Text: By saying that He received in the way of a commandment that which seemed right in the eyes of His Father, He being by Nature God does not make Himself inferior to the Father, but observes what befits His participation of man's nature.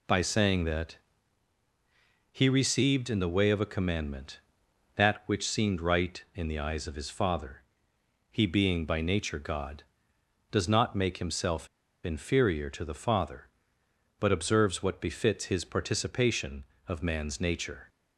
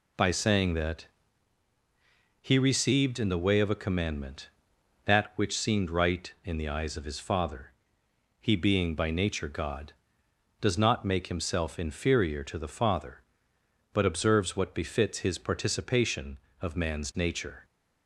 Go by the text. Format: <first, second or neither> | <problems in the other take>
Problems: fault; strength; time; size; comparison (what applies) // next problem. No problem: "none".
second | pauses between "that" and "He"; strong; at 0.9 s; 1.3 s long; strong in the second // pauses between "Himself" and "inferior"; at 11.6 s; 0.36 s long